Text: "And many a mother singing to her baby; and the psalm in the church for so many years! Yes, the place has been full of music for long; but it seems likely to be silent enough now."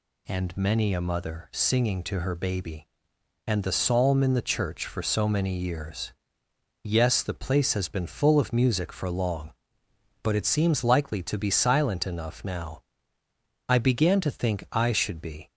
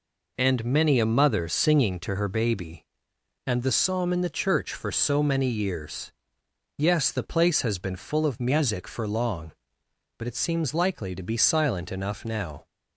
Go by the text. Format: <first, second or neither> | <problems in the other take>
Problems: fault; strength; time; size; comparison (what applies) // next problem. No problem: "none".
second | goes on to say "I began to think I should be"; strong; from 13.6 s on; 1.8 s long